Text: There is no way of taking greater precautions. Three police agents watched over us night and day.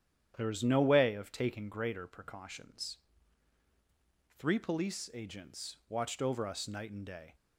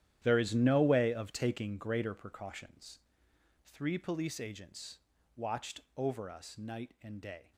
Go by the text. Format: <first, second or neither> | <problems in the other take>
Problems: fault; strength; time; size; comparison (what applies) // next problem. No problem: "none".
first | gets quieter; strong; throughout; 14 dB // starts louder than the rest; strong; until 1.2 s; 11.5 dB; strong in the first // pauses between "agents" and "watched"; slight; at 4.9 s; 0.36 s long // pauses between "watched" and "over"; slight; at 5.7 s; 0.16 s long